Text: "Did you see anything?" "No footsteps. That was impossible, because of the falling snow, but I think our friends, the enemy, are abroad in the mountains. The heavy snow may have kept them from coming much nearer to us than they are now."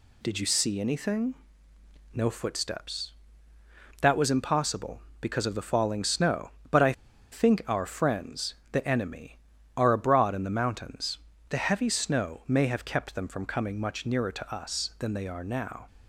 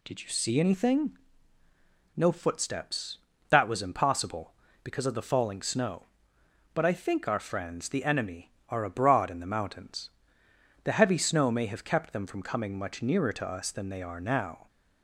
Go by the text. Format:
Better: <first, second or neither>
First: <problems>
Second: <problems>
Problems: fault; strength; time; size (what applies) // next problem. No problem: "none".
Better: second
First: pauses between "I" and "think"; at 6.9 s; 0.39 s long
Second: none